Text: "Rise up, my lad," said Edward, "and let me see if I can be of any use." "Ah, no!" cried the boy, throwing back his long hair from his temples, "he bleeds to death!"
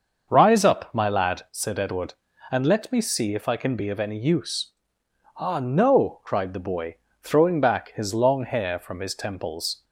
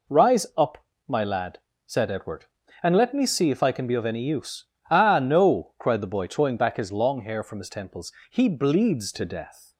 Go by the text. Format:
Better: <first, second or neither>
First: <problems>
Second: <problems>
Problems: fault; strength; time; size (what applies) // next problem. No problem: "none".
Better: second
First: starts louder than the rest; until 1.3 s; 6.5 dB // stops before "he bleeds to death"; at 9.8 s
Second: none